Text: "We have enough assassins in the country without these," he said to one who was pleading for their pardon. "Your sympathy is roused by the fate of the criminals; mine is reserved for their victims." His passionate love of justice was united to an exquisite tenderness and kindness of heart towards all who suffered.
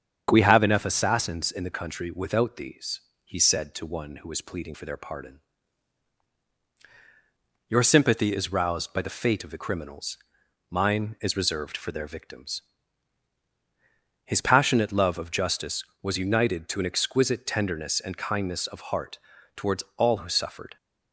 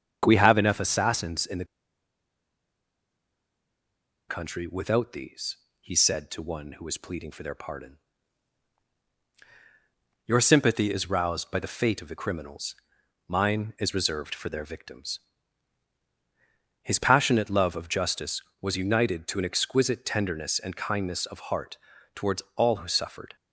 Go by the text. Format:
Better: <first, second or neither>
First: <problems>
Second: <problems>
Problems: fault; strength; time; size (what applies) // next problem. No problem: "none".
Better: first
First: starts louder than the rest; strong; until 1.3 s; 7.5 dB // pauses between "heart" and "towards"; slight; at 19.1 s; 0.36 s long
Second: starts louder than the rest; strong; until 1.2 s; 7.5 dB // pauses between "the" and "country"; strong; at 1.6 s; 2.6 s long // pauses between "heart" and "towards"; slight; at 21.7 s; 0.36 s long